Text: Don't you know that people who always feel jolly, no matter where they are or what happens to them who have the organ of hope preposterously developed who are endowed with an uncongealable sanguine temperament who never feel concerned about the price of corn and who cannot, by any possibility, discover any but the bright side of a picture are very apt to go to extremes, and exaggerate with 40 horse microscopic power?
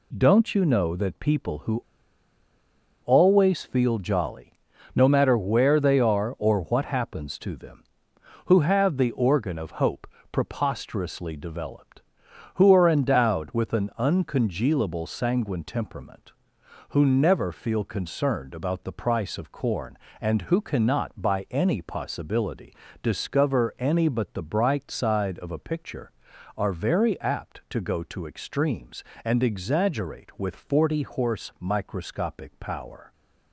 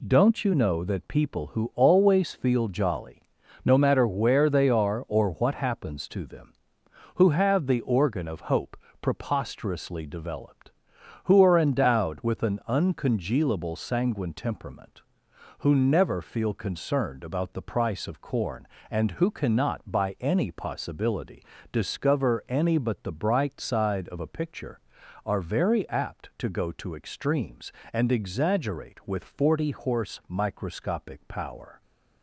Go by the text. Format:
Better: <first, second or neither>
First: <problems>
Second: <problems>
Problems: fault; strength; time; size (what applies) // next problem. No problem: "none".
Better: second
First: pauses between "who" and "always"; at 1.8 s; 1.2 s long // pauses between "hope" and "preposterously"; slight; at 10.0 s; 0.24 s long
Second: pauses between "hope" and "preposterously"; slight; at 8.7 s; 0.24 s long